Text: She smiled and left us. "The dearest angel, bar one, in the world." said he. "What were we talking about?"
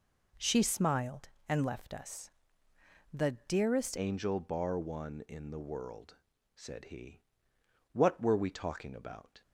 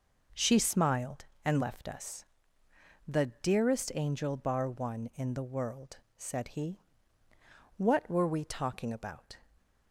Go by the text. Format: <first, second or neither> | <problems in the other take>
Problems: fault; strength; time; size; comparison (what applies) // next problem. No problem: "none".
second | pauses between "The" and "dearest"; slight; at 3.3 s; 0.16 s long; slight in the second // changes voice at "angel"; from 3.9 s on; 5.5 s long